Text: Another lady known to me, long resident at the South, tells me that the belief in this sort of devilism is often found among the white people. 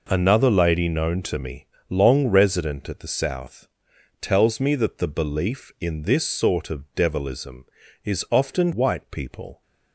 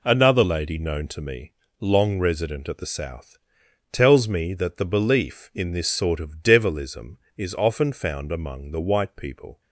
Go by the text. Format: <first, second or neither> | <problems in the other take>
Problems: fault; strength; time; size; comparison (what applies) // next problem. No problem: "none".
second | skips "found among the"; at 8.7 s